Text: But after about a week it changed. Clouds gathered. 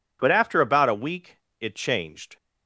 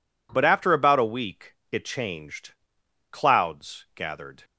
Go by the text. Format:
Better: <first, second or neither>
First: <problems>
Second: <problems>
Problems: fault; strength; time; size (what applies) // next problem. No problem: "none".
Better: second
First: pauses between "week" and "it"; slight; at 1.3 s; 0.22 s long // stops before "Clouds gathered"; at 2.3 s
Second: pauses between "week" and "it"; slight; at 1.5 s; 0.18 s long